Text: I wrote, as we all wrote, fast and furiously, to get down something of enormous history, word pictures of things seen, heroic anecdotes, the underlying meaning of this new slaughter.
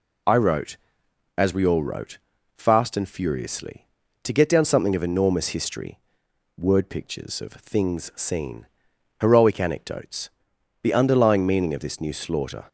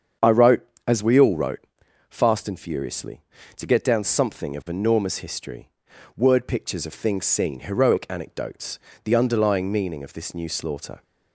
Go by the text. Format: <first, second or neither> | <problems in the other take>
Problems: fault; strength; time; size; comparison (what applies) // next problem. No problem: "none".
first | starts louder than the rest; strong; until 1.8 s; 7.5 dB